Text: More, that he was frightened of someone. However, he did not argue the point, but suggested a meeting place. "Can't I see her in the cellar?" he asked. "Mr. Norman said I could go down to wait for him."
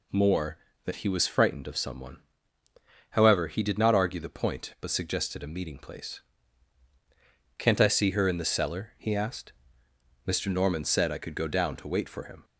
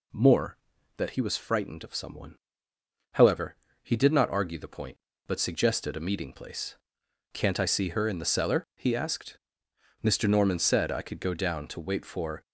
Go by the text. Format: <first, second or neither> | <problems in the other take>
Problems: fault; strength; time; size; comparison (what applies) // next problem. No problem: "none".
first | stops before "him"; at 12.4 s